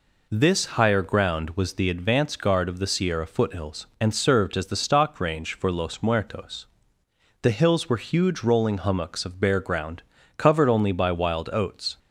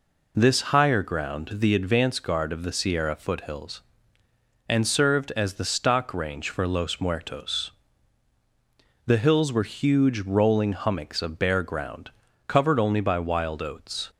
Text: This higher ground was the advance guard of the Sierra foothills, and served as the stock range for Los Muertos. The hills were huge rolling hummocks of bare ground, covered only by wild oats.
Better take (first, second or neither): first